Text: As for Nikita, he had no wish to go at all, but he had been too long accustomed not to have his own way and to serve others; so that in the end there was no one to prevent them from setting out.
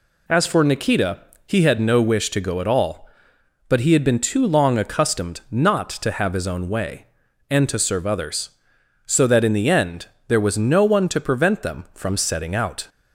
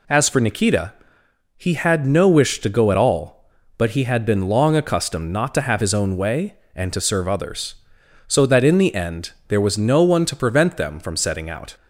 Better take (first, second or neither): first